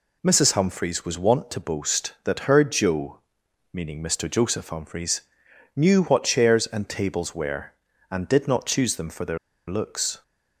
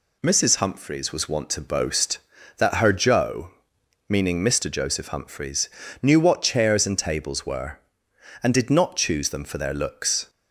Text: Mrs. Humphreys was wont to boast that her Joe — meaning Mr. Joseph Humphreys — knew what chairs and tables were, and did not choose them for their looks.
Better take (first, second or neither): second